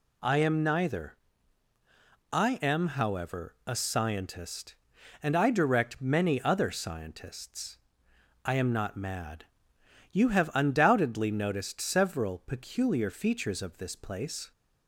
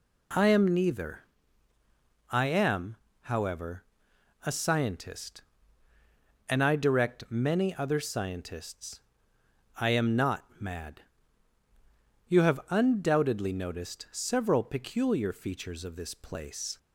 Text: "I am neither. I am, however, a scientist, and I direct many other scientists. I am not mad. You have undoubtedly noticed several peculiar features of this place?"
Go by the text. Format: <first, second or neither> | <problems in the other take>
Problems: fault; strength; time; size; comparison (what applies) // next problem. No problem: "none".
neither | none